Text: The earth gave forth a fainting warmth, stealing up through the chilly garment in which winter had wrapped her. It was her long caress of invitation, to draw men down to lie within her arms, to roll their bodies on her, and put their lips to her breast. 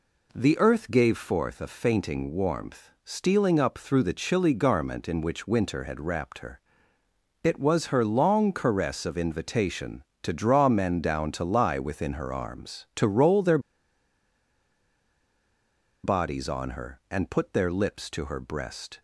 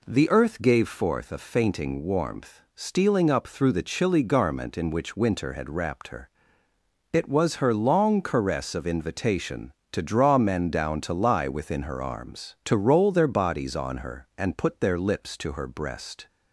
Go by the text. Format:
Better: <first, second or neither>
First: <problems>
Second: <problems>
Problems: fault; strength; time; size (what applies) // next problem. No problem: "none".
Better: second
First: pauses between "their" and "bodies"; strong; at 13.5 s; 2.4 s long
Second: none